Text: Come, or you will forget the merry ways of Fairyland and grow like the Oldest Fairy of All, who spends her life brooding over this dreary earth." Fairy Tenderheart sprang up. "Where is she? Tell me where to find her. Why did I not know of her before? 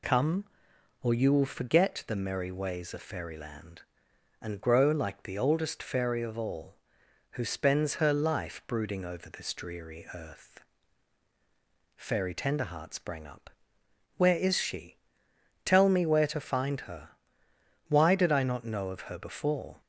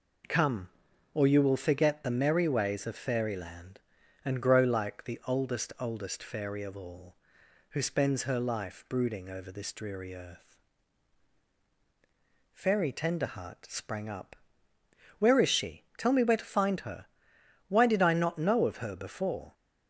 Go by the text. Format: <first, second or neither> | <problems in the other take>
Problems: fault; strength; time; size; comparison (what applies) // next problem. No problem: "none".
first | says "Oldest" twice; at 5.7 s